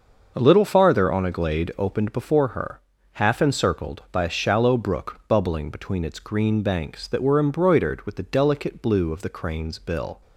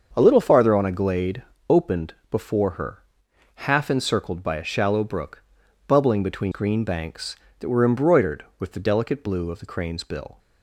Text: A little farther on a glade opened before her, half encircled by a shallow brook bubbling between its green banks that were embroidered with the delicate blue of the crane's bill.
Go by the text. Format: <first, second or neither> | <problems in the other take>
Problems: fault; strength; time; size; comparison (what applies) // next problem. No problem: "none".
first | starts louder than the rest; until 1.1 s; 6.5 dB; also in the first // pauses between "glade" and "opened"; slight; at 1.4 s; 0.28 s long // pauses between "opened" and "before"; slight; at 2.1 s; 0.18 s long // pauses between "brook" and "bubbling"; noticeable; at 5.4 s; 0.46 s long // skips "its"; at 6.5 s